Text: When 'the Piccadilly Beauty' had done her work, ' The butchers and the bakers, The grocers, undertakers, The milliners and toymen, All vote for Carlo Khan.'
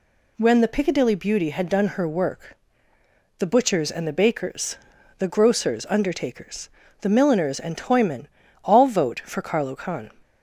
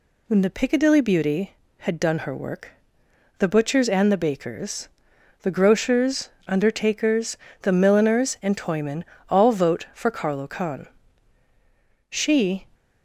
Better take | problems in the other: first | goes on to say "She"; from 12.0 s on; 0.58 s long

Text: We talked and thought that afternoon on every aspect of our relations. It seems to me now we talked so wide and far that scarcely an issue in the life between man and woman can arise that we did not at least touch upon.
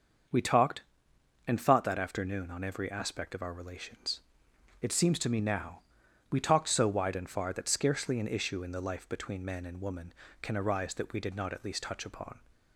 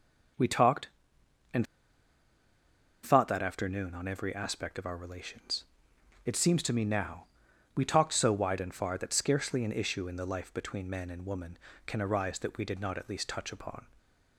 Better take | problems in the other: first | starts louder than the rest; until 3.4 s; 6.5 dB; also in the first // pauses between "and" and "thought"; strong; at 1.6 s; 1.3 s long // pauses between "now" and "we"; noticeable; at 7.2 s; 0.50 s long; noticeable in the first

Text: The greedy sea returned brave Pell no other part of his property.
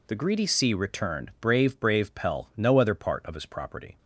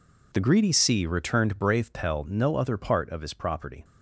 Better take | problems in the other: second | says "brave" twice; at 1.7 s

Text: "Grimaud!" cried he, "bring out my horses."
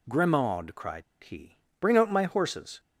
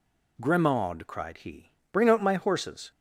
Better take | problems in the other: second | pauses between "cried" and "he"; slight; at 1.0 s; 0.20 s long

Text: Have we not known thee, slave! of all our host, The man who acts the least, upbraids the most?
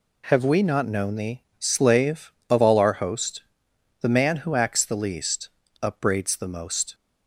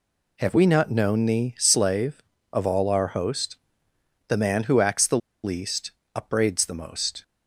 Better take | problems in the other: first | pauses between "the" and "least"; slight; at 5.1 s; 0.26 s long

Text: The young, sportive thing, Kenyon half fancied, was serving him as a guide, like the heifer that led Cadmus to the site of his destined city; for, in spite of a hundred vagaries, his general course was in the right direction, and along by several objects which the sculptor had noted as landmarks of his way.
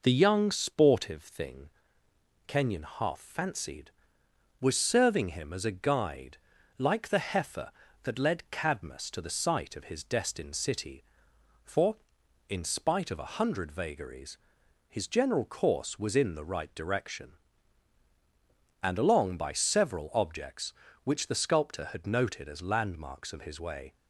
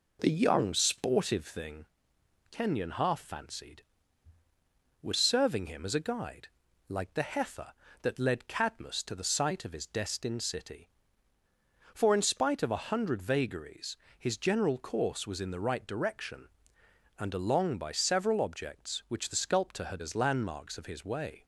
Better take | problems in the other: first | skips "noted"; at 20.0 s

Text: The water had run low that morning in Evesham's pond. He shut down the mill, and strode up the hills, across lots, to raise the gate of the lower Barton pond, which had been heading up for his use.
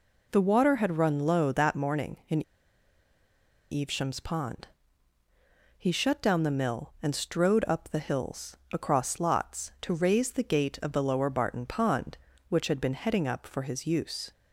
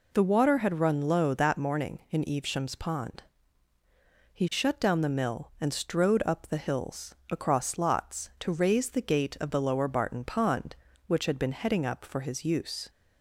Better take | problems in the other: second | pauses between "in" and "Evesham's"; strong; at 2.4 s; 1.2 s long

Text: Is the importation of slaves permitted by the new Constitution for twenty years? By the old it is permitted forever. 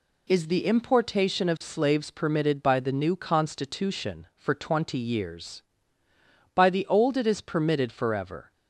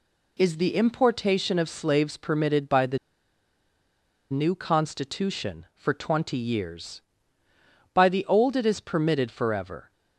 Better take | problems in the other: first | pauses between "the" and "new"; strong; at 2.9 s; 1.3 s long

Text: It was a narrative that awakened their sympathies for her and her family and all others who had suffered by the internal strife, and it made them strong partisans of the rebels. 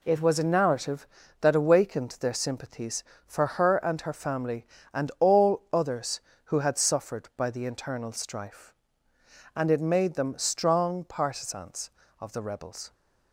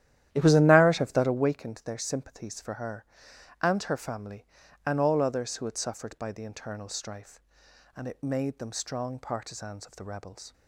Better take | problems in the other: first | starts louder than the rest; strong; until 1.4 s; 12 dB

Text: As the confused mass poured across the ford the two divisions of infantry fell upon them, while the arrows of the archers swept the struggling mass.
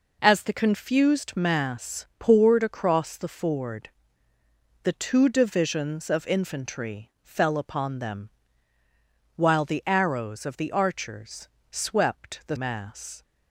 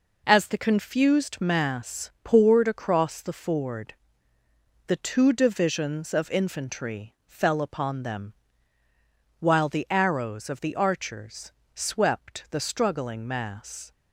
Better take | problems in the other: second | pauses between "ford" and "the"; noticeable; at 3.8 s; 0.96 s long; noticeable in the second // pauses between "archers" and "swept"; slight; at 11.4 s; 0.24 s long; slight in the second // skips "struggling"; at 12.5 s

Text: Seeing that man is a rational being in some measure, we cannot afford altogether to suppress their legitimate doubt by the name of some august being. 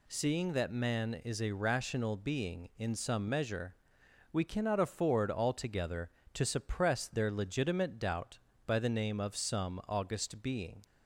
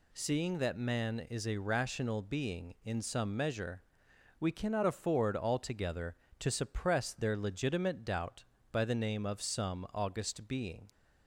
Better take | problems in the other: neither | none

